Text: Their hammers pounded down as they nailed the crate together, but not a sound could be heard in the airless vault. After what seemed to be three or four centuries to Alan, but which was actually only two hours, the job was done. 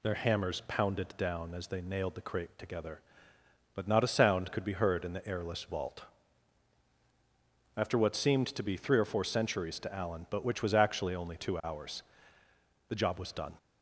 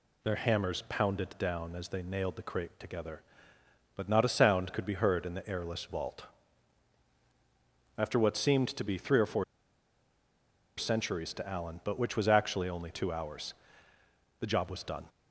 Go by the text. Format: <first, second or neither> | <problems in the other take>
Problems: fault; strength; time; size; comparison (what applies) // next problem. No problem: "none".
first | pauses between "four" and "centuries"; strong; at 9.4 s; 1.3 s long